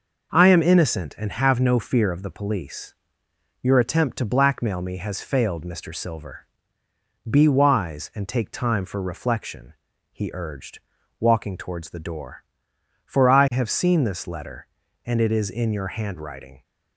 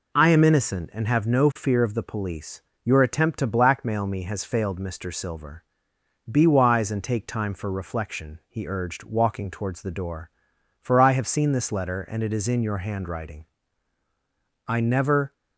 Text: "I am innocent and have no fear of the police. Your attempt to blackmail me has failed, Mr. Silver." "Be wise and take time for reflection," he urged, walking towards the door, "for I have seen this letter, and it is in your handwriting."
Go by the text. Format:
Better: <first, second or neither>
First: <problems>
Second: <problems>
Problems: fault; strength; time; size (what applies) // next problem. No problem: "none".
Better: first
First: none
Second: goes on to say "I never"; noticeable; from 14.6 s on; 0.64 s long